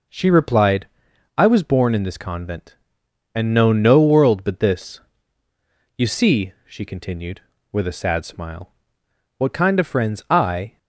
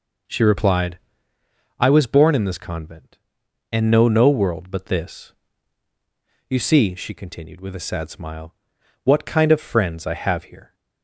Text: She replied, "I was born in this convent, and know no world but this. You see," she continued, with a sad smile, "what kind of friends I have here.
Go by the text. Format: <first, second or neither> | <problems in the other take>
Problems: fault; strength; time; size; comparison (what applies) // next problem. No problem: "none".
second | stops before "have here"; at 10.7 s